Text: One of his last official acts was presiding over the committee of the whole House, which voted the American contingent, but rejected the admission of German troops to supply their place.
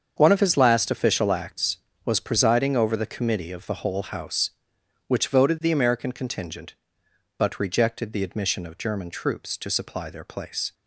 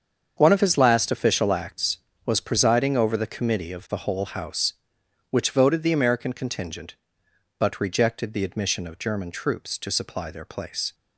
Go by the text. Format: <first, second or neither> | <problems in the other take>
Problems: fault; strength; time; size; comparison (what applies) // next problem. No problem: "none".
neither | starts louder than the rest; strong; the same in both